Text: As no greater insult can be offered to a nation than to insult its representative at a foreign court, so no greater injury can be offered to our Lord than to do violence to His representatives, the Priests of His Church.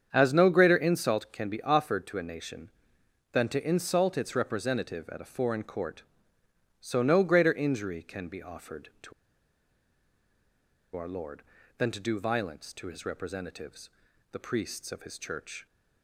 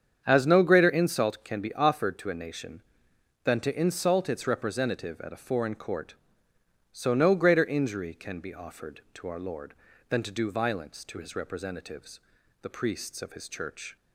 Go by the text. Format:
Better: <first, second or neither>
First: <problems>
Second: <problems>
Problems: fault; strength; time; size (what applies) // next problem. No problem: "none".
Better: second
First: starts louder than the rest; strong; until 1.1 s; 8 dB // pauses between "to" and "our"; strong; at 9.1 s; 1.8 s long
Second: starts louder than the rest; strong; until 1.2 s; 8 dB